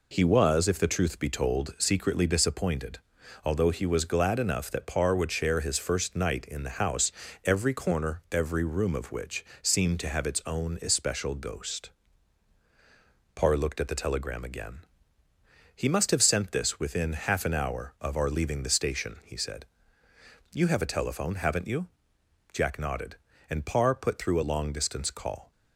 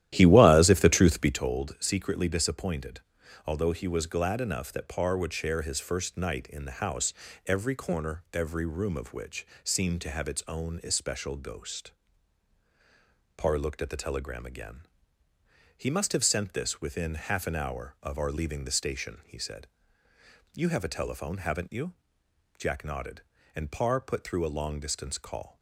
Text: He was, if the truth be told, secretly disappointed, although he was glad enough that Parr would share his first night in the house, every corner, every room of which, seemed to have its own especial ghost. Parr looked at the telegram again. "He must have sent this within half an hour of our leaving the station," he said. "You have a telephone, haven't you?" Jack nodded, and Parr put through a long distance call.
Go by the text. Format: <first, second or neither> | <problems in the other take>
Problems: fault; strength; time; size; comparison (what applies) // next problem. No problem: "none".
first | starts louder than the rest; strong; until 1.4 s; 12.5 dB